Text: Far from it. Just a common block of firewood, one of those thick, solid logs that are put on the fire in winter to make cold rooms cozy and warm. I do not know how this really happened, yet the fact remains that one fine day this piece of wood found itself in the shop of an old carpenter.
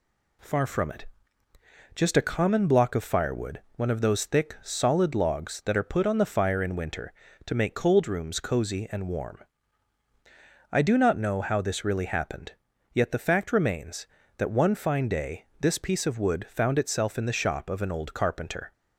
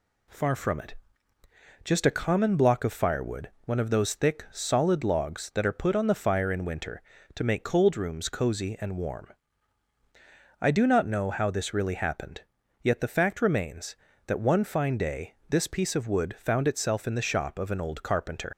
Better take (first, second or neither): first